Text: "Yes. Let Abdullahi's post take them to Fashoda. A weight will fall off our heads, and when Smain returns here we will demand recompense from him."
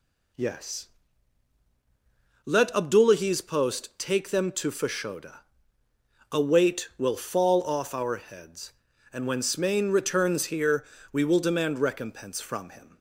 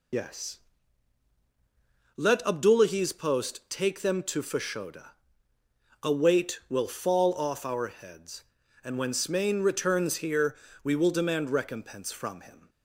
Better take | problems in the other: first | loses the start of "Yes"; at 0.1 s; 60 ms // pauses between "here" and "we"; slight; at 10.5 s; 0.28 s long; slight in the first

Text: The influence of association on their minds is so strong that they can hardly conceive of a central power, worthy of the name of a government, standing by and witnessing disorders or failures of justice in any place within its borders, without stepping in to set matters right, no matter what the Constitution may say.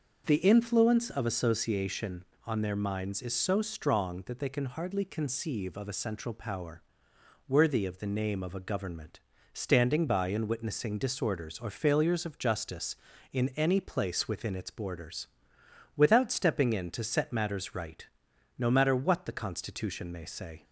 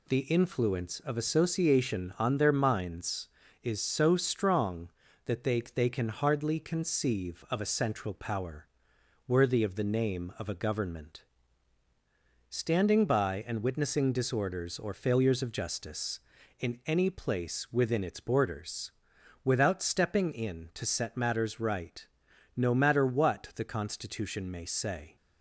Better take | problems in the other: first | says "they" twice; at 5.6 s

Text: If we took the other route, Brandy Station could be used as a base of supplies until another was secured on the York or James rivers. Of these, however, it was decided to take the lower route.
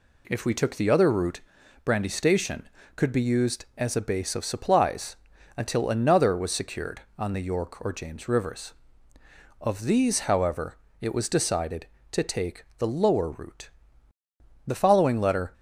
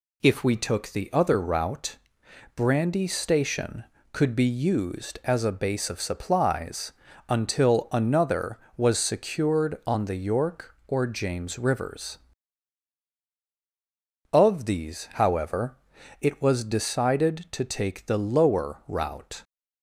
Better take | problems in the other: second | pauses between "supplies" and "until"; at 5.1 s; 0.40 s long; also in the second // goes on to say "The following letter"; noticeable; from 14.6 s on; 0.86 s long

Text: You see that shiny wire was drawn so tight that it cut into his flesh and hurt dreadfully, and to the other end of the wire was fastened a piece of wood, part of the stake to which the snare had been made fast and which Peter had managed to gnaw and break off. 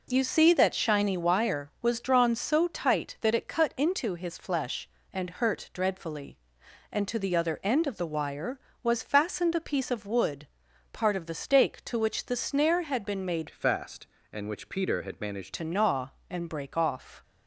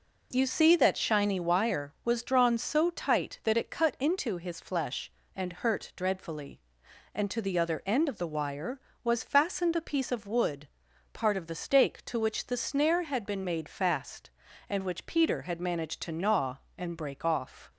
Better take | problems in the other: second | changes voice from "fast" to "managed"; from 13.5 to 15.5 s; 2.0 s long

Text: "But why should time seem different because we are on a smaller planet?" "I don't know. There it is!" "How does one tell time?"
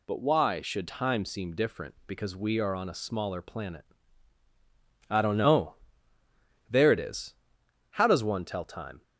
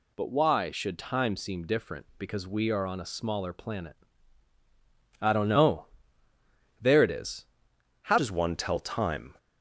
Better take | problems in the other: first | changes voice at "does"; from 8.1 s on; 1.2 s long

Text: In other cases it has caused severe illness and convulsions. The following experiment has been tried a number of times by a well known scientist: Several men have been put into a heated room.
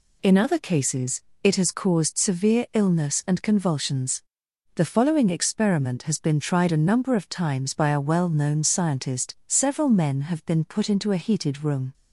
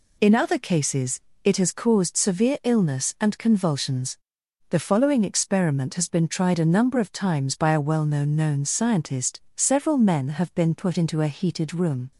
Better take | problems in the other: first | pauses between "cases" and "it"; slight; at 1.2 s; 0.24 s long; slight in the first // says "known" twice; at 8.3 s

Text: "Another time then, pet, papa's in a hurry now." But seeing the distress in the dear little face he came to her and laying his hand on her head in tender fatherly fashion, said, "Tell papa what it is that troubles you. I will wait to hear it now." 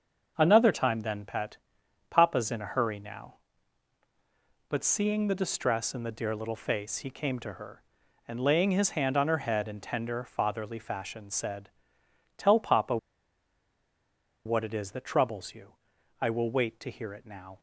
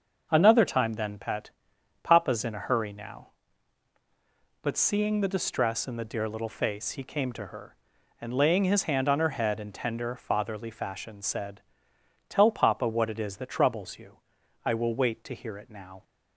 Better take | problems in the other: second | starts louder than the rest; until 1.3 s; 6.5 dB; also in the second // pauses between "papa" and "what"; strong; at 12.9 s; 1.4 s long

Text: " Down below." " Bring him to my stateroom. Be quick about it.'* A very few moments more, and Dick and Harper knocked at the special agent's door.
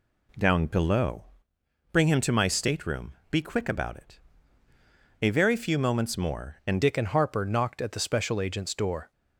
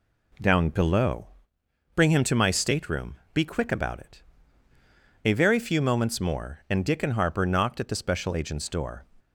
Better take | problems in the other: second | changes voice at "Dick"; from 6.8 s on; 2.3 s long

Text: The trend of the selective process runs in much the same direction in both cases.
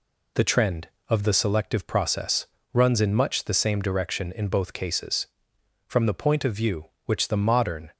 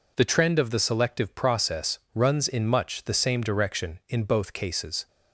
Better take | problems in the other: second | pauses between "process" and "runs"; slight; at 2.4 s; 0.26 s long; slight in the second // goes on to say "From the point of view which the modern"; strong; from 5.8 s on; 2.0 s long

